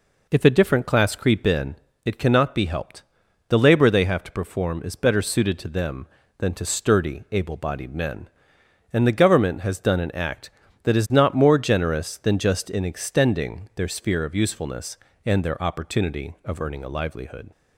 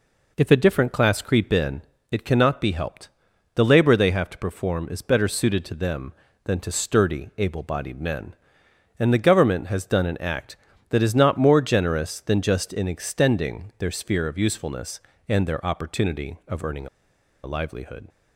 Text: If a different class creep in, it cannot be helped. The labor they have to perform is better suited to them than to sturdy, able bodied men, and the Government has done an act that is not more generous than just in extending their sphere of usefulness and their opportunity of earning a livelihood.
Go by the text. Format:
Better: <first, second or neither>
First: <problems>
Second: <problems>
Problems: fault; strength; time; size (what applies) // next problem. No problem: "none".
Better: first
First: none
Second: pauses between "earning" and "a"; noticeable; at 16.8 s; 0.55 s long